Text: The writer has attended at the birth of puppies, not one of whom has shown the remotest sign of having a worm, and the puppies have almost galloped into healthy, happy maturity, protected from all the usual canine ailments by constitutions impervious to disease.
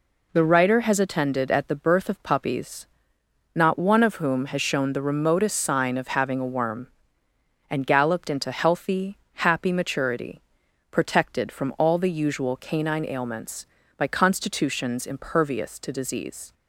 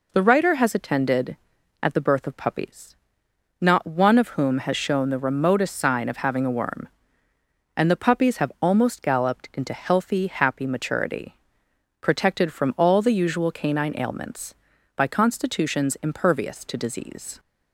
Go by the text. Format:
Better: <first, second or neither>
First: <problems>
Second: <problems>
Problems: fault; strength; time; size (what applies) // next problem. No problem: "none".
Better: second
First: skips "the puppies have almost"; at 7.8 s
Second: none